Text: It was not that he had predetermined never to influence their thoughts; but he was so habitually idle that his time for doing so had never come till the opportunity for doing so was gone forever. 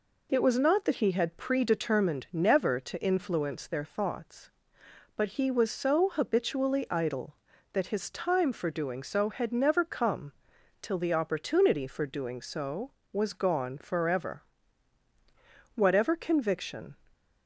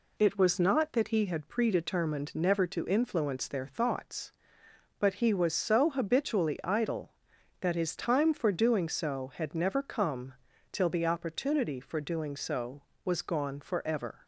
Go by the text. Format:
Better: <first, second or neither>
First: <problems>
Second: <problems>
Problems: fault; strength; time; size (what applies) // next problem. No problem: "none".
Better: second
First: pauses between "come" and "till"; noticeable; at 10.3 s; 0.50 s long // goes on to say "Whatever conviction"; noticeable; from 15.7 s on; 1.2 s long // stays silent after the last word; slight; from 16.9 s on; 0.5 s long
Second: pauses between "come" and "till"; at 10.3 s; 0.40 s long